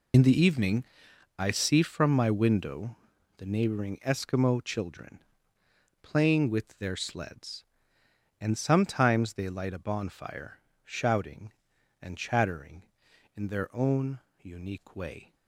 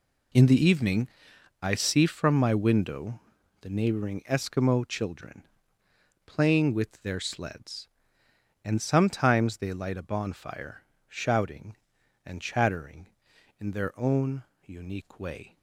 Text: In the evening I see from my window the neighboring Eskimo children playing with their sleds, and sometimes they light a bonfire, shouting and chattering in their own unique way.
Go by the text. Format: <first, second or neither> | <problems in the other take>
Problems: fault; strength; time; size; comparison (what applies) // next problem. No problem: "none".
second | loses the start of "In"; at 0.1 s; 45 ms // pauses between "evening" and "I"; noticeable; at 0.8 s; 0.54 s long; noticeable in the second // pauses between "window" and "the"; at 2.9 s; 0.42 s long; also in the second // pauses between "children" and "playing"; noticeable; at 5.2 s; 0.80 s long; noticeable in the second // pauses between "own" and "unique"; slight; at 14.1 s; 0.22 s long; slight in the second